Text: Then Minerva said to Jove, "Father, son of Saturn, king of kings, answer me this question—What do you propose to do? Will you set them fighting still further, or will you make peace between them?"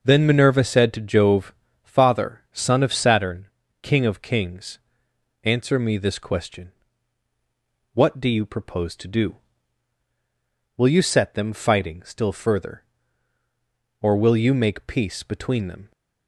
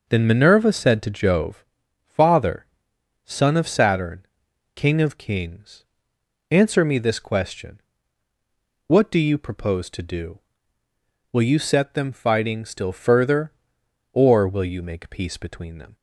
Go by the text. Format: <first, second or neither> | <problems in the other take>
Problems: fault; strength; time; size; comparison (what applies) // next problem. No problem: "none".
neither | none